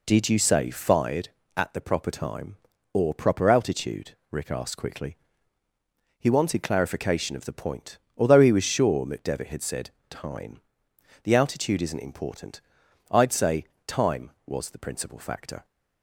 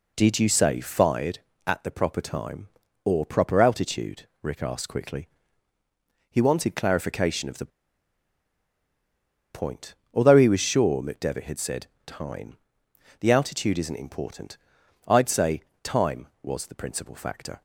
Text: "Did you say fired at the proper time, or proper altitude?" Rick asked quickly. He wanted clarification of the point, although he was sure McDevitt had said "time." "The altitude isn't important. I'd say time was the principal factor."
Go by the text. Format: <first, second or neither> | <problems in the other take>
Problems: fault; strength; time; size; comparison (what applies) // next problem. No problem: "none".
first | pauses between "the" and "point"; strong; at 7.7 s; 1.8 s long // pauses between "said" and "time"; slight; at 11.8 s; 0.18 s long; slight in the first // pauses between "say" and "time"; slight; at 15.6 s; 0.22 s long; slight in the first